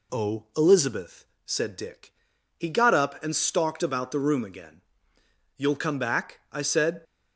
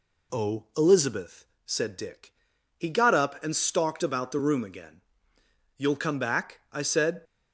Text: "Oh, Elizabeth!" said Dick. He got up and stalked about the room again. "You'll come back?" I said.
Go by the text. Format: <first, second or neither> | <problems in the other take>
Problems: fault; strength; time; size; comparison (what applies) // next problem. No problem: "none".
neither | none